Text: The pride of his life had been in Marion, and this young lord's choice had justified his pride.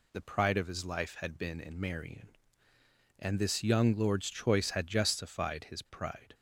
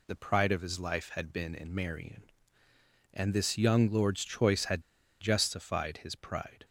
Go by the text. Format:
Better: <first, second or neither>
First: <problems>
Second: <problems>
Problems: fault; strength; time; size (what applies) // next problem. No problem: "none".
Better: first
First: none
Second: pauses between "had" and "justified"; at 4.8 s; 0.39 s long